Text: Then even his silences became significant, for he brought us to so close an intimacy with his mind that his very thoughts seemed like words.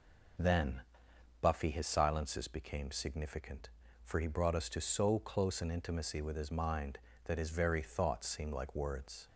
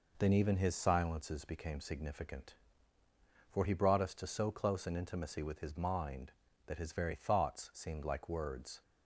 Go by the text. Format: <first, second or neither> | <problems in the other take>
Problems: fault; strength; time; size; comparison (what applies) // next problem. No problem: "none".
second | says "buffy" for "even"; at 1.4 s